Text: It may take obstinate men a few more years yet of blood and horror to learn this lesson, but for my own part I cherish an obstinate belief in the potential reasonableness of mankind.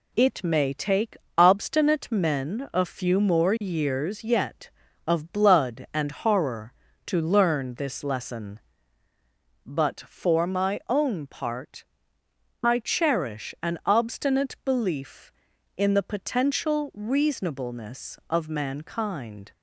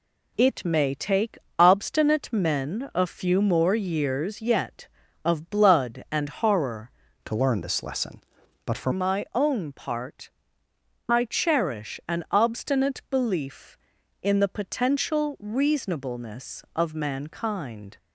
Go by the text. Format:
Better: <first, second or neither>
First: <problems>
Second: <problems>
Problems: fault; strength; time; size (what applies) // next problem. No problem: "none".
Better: first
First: pauses between "take" and "obstinate"; slight; at 1.1 s; 0.22 s long // pauses between "part" and "I"; noticeable; at 11.8 s; 0.80 s long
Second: pauses between "take" and "obstinate"; slight; at 1.3 s; 0.22 s long // changes voice from "to" to "for"; from 7.2 to 8.9 s; 1.7 s long // pauses between "part" and "I"; noticeable; at 10.2 s; 0.80 s long